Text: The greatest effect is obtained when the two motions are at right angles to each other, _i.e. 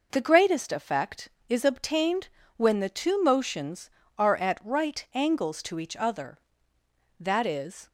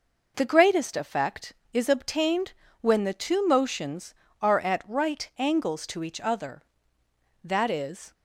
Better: neither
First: pauses between "obtained" and "when"; slight; at 2.2 s; 0.30 s long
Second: pauses between "obtained" and "when"; slight; at 2.5 s; 0.30 s long

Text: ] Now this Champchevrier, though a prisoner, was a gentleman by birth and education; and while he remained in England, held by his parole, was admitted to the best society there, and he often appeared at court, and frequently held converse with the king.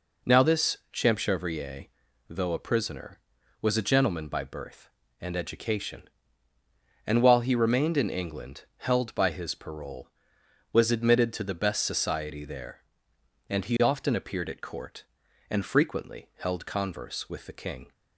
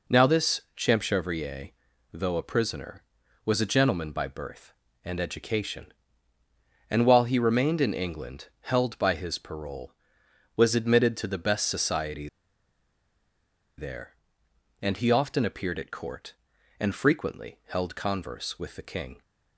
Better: first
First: pauses between "this" and "Champchevrier"; slight; at 0.7 s; 0.16 s long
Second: pauses between "this" and "Champchevrier"; slight; at 0.6 s; 0.16 s long // pauses between "society" and "there"; strong; at 12.2 s; 1.4 s long

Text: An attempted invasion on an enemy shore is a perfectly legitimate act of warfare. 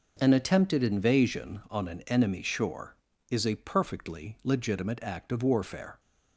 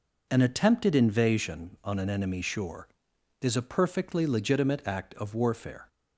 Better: neither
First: none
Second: none

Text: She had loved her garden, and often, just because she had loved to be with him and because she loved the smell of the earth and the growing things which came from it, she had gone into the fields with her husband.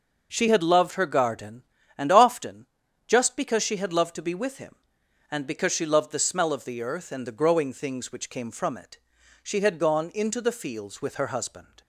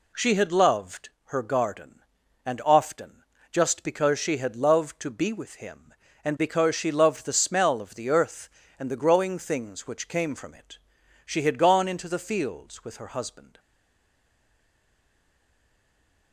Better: first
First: none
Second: pauses between "loved" and "her"; slight; at 1.0 s; 0.16 s long // stays silent after the last word; strong; from 13.5 s on; 2.8 s long

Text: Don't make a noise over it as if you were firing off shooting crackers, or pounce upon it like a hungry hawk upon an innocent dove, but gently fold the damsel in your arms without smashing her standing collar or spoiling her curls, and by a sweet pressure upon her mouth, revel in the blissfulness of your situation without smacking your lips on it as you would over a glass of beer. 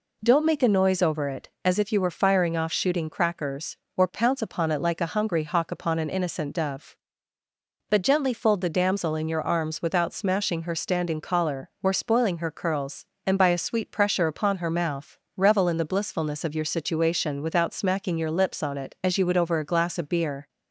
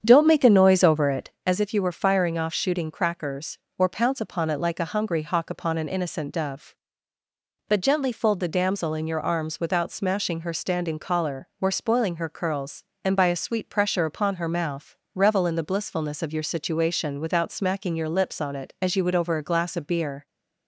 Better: first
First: none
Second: starts louder than the rest; strong; until 1.4 s; 8 dB

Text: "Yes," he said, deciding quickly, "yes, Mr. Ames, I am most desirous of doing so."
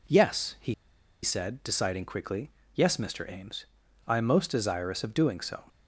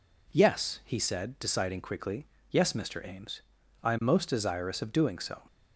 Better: second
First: pauses between "he" and "said"; noticeable; at 0.7 s; 0.49 s long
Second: none

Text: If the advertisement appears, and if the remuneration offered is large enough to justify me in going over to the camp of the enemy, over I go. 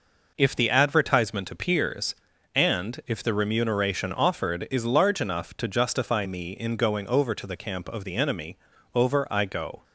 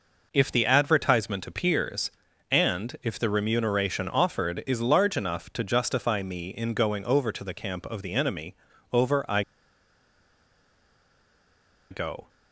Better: first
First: none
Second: pauses between "I" and "go"; strong; at 9.4 s; 2.4 s long

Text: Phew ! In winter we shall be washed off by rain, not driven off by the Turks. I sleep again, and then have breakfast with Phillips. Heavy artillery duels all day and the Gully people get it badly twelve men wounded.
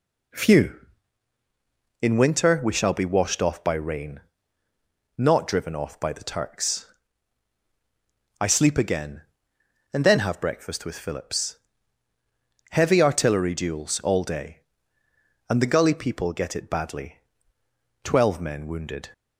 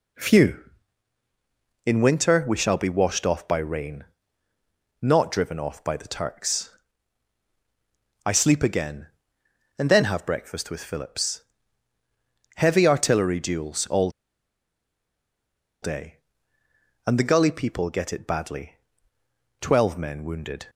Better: first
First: pauses between "badly" and "twelve"; noticeable; at 17.1 s; 0.84 s long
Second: pauses between "all" and "day"; strong; at 14.0 s; 1.7 s long // pauses between "badly" and "twelve"; noticeable; at 18.7 s; 0.84 s long

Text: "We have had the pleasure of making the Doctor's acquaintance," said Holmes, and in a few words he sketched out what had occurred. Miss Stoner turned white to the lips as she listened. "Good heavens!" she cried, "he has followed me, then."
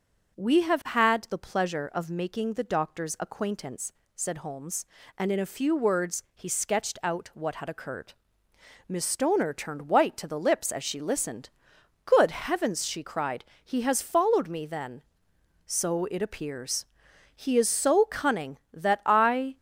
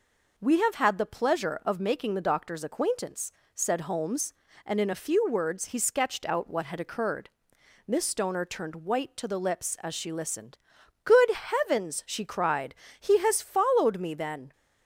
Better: second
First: goes on to say "So it appears He is so cunning that I"; strong; from 15.6 s on; 3.9 s long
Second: none

